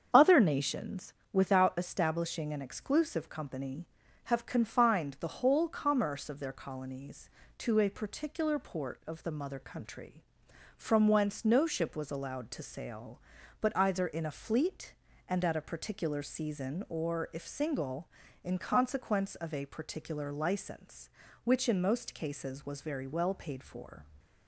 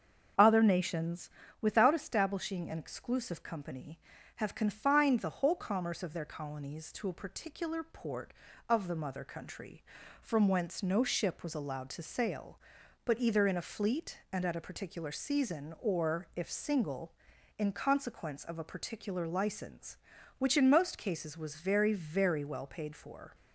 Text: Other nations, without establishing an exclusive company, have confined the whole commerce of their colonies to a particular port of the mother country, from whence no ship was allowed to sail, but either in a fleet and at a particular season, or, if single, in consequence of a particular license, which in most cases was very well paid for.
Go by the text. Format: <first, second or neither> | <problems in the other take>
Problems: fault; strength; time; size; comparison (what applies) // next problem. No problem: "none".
first | starts louder than the rest; strong; until 1.6 s; 7 dB; strong in the first // says "very" twice; at 21.9 s